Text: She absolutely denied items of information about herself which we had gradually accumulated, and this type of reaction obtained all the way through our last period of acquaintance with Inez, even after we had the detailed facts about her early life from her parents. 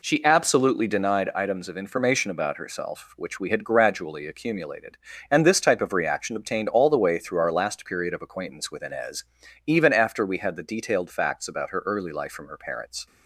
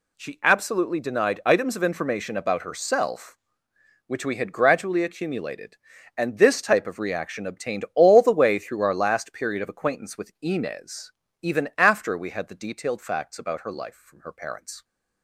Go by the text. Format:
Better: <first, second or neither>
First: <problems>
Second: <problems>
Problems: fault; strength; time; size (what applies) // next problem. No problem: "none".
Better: first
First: none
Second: skips "early"; at 13.7 s